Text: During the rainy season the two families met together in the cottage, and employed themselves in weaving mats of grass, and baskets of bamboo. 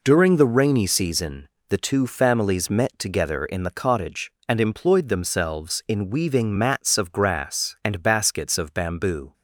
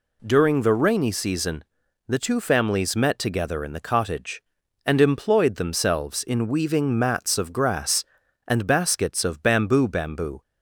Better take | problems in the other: first | pauses between "season" and "the"; noticeable; at 1.6 s; 0.46 s long; slight in the first // says "bamboo" twice; at 9.8 s

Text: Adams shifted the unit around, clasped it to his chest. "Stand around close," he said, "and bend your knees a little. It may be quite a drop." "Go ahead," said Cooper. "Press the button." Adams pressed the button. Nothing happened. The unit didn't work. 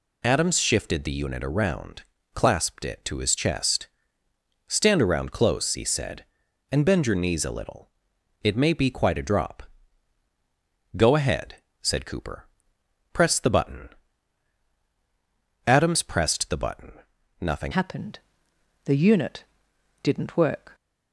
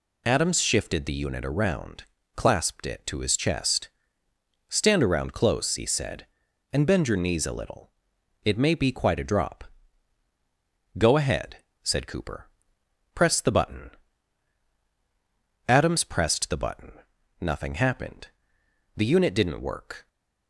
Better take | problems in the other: second | changes voice at "happened"; from 17.7 s on; 3.0 s long // pauses between "unit" and "didn't"; noticeable; at 19.4 s; 0.60 s long

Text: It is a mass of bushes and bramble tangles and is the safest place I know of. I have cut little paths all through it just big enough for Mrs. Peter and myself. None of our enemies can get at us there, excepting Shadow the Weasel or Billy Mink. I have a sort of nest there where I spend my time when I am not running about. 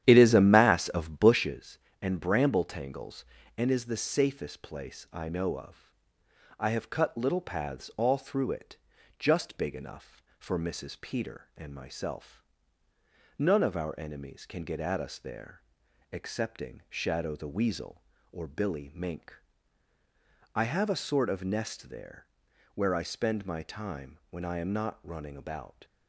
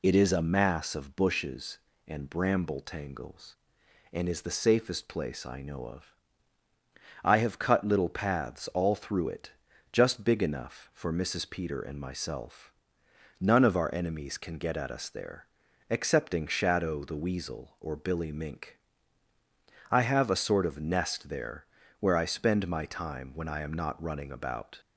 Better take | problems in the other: second | starts louder than the rest; strong; until 1.4 s; 10.5 dB // pauses between "it" and "just"; at 8.7 s; 0.42 s long; also in the second // pauses between "there" and "where"; noticeable; at 22.2 s; 0.48 s long; slight in the second

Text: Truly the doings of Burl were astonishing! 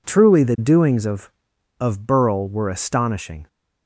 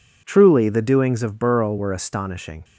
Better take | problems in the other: second | says "of" twice; at 1.7 s

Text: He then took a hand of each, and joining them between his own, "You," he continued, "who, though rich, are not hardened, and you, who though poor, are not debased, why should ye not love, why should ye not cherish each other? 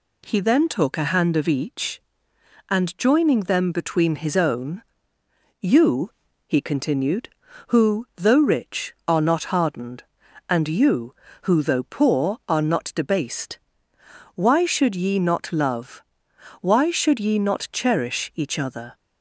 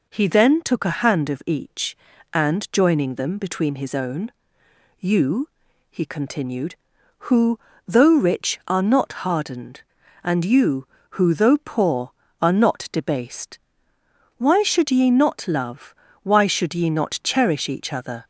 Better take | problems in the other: neither | none

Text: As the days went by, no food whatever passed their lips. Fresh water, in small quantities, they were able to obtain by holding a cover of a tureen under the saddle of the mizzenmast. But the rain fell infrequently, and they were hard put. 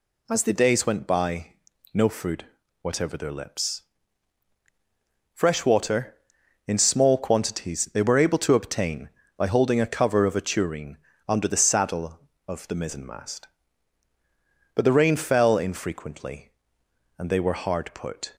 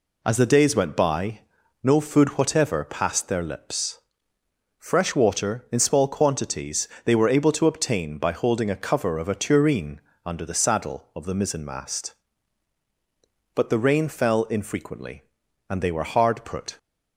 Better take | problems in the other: second | pauses between "food" and "whatever"; slight; at 2.4 s; 0.36 s long // skips "passed"; at 3.1 s // pauses between "tureen" and "under"; slight; at 10.9 s; 0.30 s long; slight in the second

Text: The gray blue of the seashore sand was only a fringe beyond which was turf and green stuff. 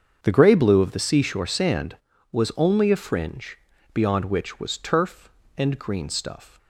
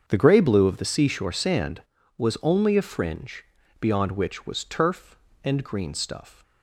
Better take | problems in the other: neither | starts louder than the rest; the same in both // pauses between "fringe" and "beyond"; slight; the same in both

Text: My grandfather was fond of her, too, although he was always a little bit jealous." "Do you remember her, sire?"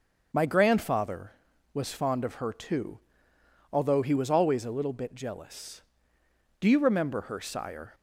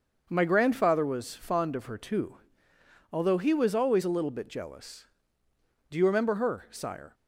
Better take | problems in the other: neither | starts louder than the rest; the same in both

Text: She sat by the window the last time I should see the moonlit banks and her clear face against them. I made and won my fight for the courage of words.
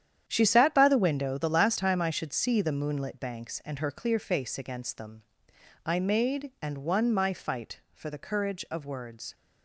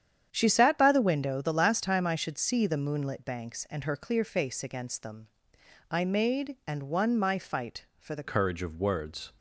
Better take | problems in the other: first | starts louder than the rest; strong; until 1.3 s; 9 dB; strong in the first // changes voice at "courage"; from 8.2 s on; 1.1 s long

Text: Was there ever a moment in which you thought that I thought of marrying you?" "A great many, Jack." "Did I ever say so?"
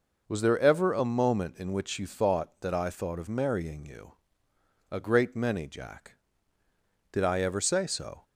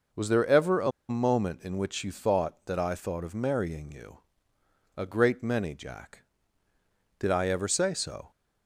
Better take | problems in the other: first | pauses between "a" and "moment"; slight; at 0.9 s; 0.19 s long

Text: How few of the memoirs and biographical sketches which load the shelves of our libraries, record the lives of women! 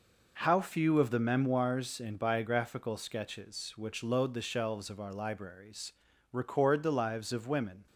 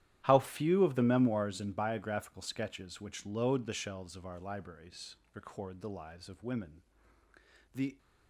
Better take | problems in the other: first | starts louder than the rest; strong; until 1.2 s; 12 dB // goes on to say "The"; slight; from 7.7 s on; 0.22 s long

